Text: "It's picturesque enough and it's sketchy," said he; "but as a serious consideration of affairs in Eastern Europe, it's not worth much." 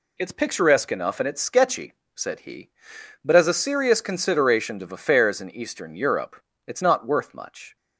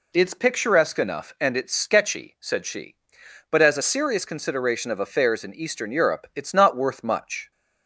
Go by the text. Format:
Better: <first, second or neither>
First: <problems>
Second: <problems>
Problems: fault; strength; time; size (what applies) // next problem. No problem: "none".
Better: first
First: none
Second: says "she" for "he"; at 2.6 s